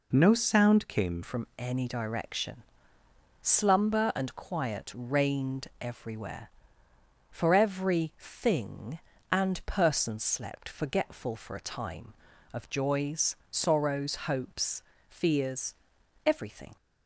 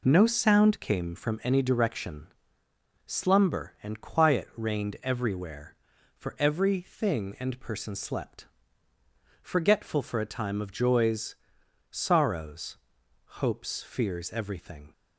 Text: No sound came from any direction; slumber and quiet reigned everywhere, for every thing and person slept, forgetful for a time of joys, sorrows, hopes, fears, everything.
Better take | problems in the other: second | changes voice at "from"; from 1.2 s on; 15.5 s long

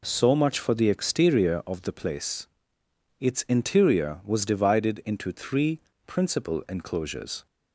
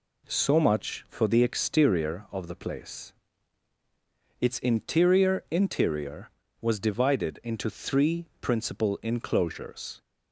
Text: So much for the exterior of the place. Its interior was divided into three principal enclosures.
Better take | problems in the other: first | says "interior" twice; at 5.5 s // pauses between "three" and "principal"; slight; at 8.2 s; 0.16 s long; slight in the first

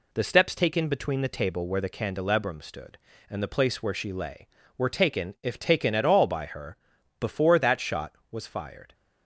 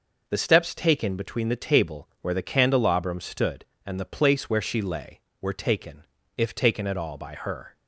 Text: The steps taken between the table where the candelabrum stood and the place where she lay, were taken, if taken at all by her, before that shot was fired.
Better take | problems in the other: first | stops before "before that shot was fired"; at 7.7 s

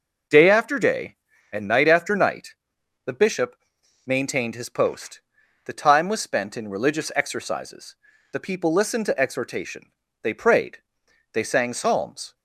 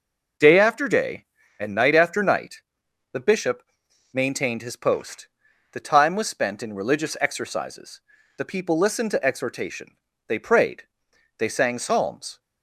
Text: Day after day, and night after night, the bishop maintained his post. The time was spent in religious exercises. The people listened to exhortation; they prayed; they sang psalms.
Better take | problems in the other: neither | pauses between "bishop" and "maintained"; noticeable; the same in both

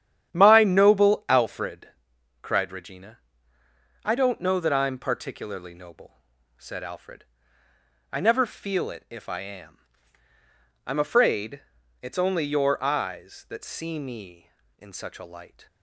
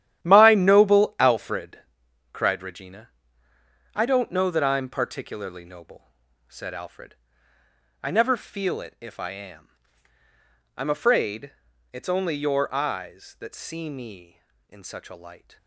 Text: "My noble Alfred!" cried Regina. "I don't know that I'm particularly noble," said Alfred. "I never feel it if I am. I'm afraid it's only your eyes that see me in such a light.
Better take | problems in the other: first | gets quieter; strong; throughout; 11.5 dB // starts louder than the rest; strong; until 1.2 s; 11.5 dB; strong in the first // pauses between "afraid" and "it's"; at 11.5 s; 0.38 s long; also in the first

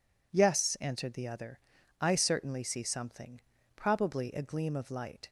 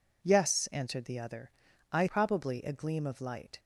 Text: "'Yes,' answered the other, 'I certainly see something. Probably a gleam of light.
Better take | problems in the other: first | skips "certainly see something"; at 2.0 s

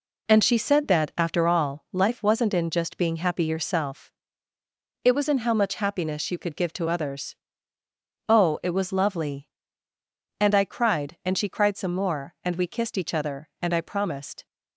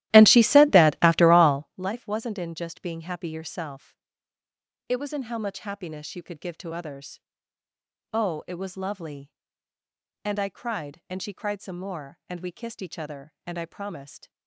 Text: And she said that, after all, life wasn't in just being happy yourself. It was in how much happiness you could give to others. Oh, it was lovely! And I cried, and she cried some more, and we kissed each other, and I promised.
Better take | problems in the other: first | starts louder than the rest; strong; until 1.8 s; 15 dB

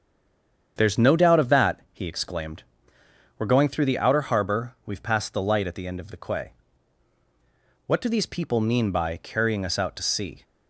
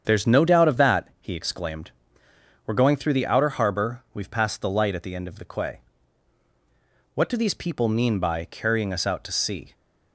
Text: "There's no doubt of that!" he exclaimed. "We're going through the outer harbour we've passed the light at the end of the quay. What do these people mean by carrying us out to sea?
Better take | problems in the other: second | stays silent before the first word; slight; until 0.7 s; 0.7 s long // starts louder than the rest; strong; until 1.7 s; 8 dB; strong in the second

